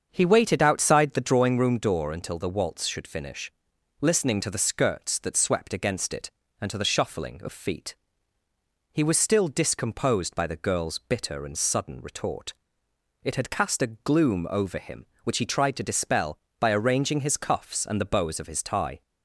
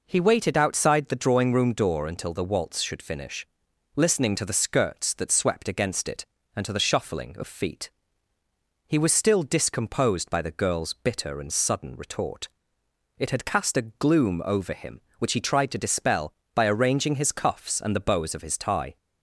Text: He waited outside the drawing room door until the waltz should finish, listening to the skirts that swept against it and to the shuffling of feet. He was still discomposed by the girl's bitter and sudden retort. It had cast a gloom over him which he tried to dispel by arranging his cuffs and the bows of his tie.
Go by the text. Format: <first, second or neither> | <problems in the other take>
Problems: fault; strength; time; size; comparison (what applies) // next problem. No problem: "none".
second | starts louder than the rest; strong; until 1.6 s; 7.5 dB